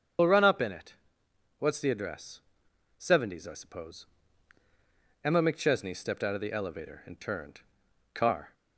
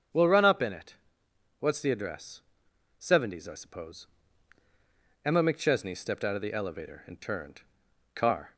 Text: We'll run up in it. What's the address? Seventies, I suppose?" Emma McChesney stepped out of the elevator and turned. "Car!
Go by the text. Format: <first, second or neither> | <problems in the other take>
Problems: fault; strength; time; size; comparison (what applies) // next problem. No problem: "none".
second | loses the start of "We'll"; at 0.1 s; 60 ms // starts louder than the rest; until 1.8 s; 7 dB; strong in the second